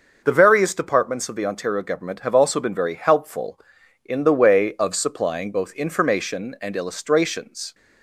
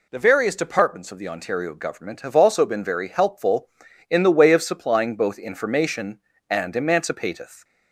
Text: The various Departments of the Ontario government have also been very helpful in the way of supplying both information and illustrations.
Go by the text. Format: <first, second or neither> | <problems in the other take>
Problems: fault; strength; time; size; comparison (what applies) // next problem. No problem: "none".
first | says "emancipateth" for "illustrations"; at 6.7 s